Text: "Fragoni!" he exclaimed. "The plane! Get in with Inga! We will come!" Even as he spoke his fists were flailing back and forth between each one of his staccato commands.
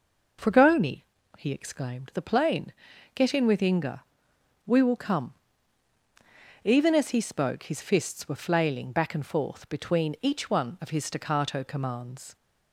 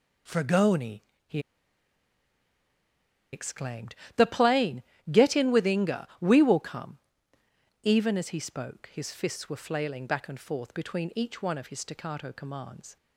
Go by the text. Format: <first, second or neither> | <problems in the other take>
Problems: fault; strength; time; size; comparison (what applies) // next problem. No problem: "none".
first | pauses between "he" and "exclaimed"; strong; at 1.3 s; 1.9 s long